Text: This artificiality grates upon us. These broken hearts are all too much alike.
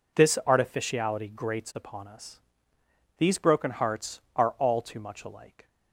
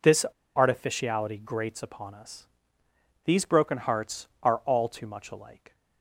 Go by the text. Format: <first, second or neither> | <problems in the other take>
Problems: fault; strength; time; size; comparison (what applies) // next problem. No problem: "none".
first | pauses between "This" and "artificiality"; slight; at 0.2 s; 0.31 s long